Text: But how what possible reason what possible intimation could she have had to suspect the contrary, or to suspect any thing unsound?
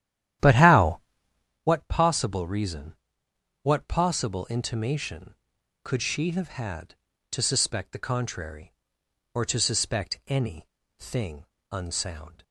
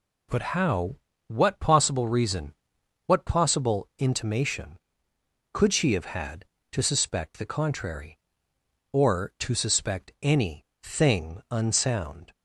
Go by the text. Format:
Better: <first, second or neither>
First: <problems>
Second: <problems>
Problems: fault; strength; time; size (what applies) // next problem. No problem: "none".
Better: second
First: starts louder than the rest; strong; until 1.7 s; 11.5 dB // pauses between "how" and "what"; noticeable; at 1.0 s; 0.64 s long // pauses between "reason" and "what"; noticeable; at 2.9 s; 0.66 s long // pauses between "any" and "thing"; slight; at 10.6 s; 0.30 s long // pauses between "thing" and "unsound"; slight; at 11.4 s; 0.26 s long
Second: pauses between "how" and "what"; slight; at 0.9 s; 0.30 s long // pauses between "reason" and "what"; noticeable; at 2.5 s; 0.54 s long // pauses between "any" and "thing"; slight; at 10.6 s; 0.18 s long